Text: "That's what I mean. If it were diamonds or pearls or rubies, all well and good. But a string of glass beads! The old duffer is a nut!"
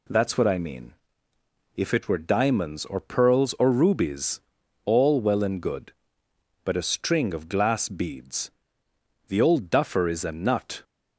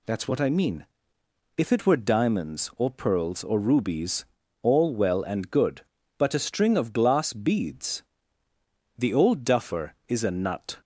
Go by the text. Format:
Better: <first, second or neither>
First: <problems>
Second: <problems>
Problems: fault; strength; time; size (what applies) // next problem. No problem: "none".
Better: neither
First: none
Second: none